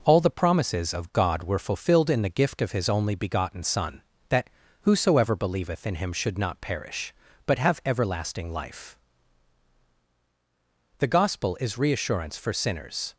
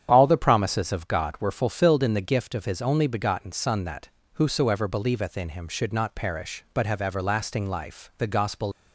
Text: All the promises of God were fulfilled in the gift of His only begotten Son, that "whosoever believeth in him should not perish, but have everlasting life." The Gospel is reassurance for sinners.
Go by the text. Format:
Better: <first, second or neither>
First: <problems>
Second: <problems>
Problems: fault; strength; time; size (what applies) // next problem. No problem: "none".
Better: first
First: pauses between "that" and "whosoever"; slight; at 4.5 s; 0.32 s long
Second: starts louder than the rest; strong; until 1.1 s; 9 dB // pauses between "that" and "whosoever"; slight; at 4.0 s; 0.26 s long // stops before "is reassurance for sinners"; at 8.7 s